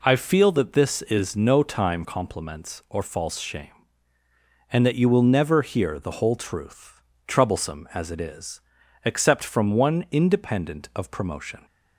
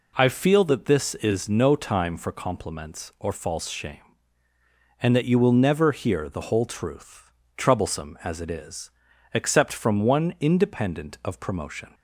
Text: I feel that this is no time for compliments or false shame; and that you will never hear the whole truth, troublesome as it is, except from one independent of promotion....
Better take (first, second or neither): second